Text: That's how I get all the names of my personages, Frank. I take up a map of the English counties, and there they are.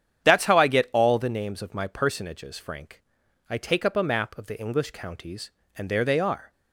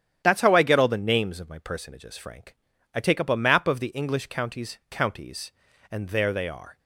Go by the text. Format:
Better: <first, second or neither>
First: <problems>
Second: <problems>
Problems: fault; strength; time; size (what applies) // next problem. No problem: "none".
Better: first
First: starts louder than the rest; strong; until 1.2 s; 9 dB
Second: starts louder than the rest; strong; until 1.2 s; 10 dB // says "counties" twice; at 4.9 s